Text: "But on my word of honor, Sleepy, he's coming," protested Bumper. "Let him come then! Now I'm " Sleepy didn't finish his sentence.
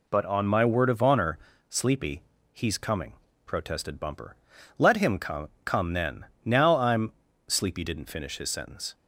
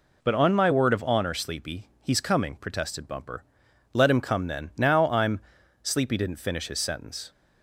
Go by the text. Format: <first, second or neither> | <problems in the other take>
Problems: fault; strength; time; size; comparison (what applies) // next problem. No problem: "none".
second | says "come" twice; at 5.6 s